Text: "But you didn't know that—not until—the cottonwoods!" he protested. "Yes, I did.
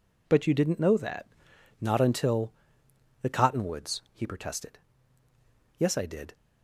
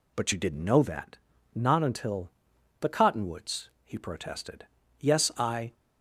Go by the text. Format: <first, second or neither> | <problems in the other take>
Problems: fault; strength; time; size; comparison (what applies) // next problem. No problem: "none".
first | stops before "did"; at 5.7 s